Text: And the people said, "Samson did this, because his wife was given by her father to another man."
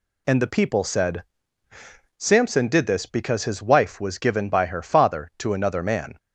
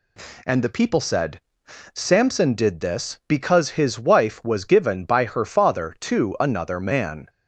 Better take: neither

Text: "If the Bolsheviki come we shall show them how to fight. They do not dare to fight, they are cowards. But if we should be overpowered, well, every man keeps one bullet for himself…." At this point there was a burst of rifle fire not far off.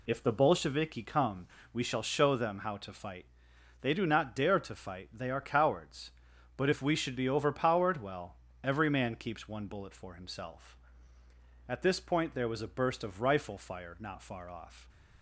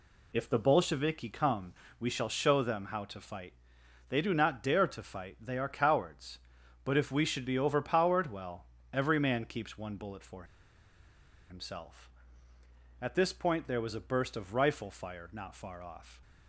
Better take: first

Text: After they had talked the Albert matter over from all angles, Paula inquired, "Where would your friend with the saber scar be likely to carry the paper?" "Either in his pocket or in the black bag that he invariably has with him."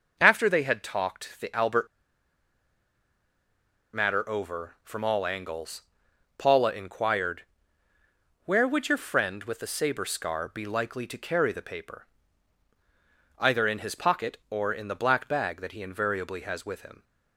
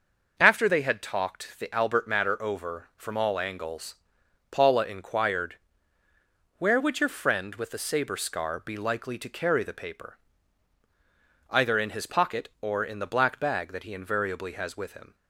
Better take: second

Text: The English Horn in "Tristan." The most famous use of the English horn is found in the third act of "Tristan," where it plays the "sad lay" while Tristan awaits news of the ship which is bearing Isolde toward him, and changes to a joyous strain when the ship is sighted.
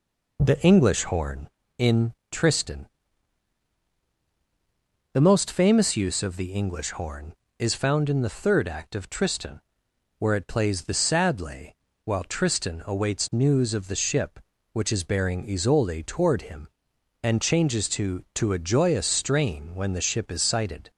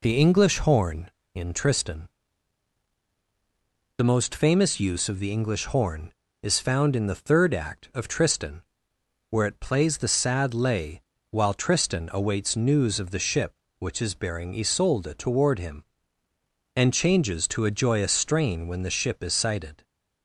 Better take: second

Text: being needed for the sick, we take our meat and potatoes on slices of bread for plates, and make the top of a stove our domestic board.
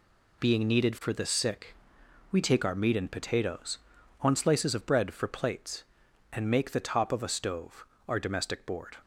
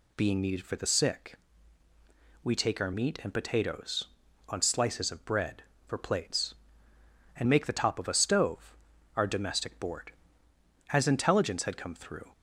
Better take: first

